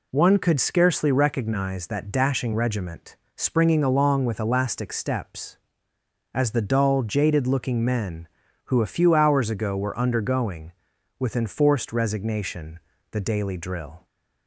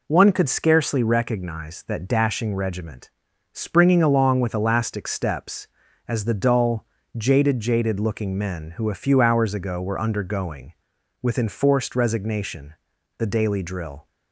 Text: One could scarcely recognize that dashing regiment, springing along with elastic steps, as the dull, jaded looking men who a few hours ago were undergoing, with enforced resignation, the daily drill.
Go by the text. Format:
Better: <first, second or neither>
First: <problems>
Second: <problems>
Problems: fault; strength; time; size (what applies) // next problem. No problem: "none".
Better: first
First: none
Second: says "jaded" twice; at 7.5 s